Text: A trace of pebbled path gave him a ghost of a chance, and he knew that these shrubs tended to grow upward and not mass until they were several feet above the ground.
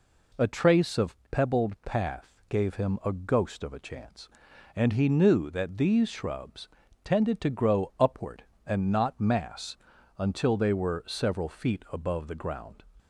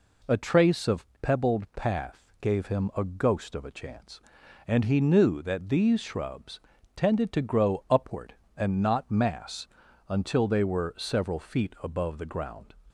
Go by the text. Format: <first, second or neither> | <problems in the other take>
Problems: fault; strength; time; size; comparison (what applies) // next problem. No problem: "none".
neither | pauses between "of" and "pebbled"; slight; the same in both // pauses between "shrubs" and "tended"; slight; the same in both // pauses between "mass" and "until"; the same in both